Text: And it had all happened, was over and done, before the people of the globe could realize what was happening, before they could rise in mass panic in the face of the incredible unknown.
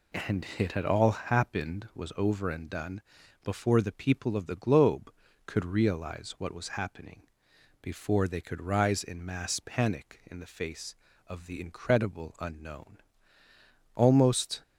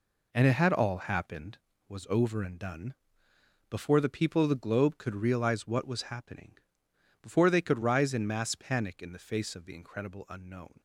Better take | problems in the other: second | goes on to say "Almost"; noticeable; from 13.9 s on; 0.66 s long

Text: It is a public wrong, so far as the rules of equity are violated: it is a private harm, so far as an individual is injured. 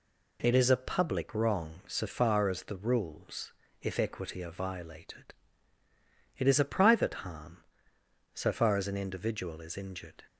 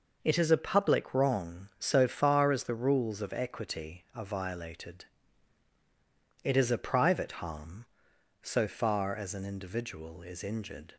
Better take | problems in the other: second | says "if" for "of"; at 3.8 s

